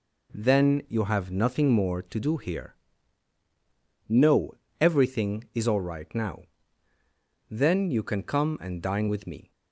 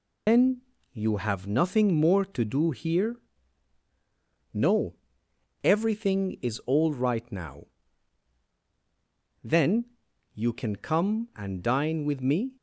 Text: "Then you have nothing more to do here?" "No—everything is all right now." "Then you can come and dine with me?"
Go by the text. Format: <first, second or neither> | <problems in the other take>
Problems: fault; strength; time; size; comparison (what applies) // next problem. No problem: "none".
first | loses the start of "Then"; at 0.2 s; 150 ms // pauses between "Then" and "you"; slight; at 0.6 s; 0.30 s long // pauses between "Then" and "you"; noticeable; at 9.8 s; 0.48 s long